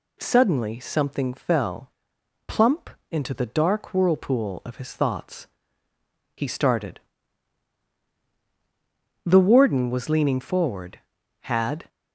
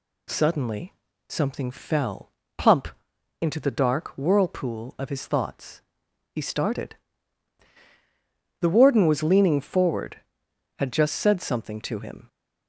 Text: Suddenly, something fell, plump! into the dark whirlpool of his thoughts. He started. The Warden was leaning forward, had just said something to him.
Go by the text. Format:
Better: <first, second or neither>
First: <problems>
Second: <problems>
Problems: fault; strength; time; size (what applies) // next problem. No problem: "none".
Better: second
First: stops before "just said something to him"; at 11.8 s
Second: none